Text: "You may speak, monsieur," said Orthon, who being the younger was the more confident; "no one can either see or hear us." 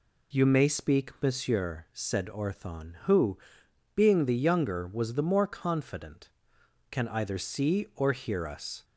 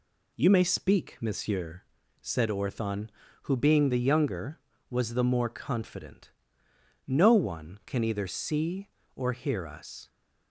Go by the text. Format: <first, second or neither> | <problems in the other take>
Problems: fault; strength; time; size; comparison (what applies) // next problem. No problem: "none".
second | pauses between "who" and "being"; noticeable; at 3.3 s; 0.58 s long // skips "no one"; at 6.6 s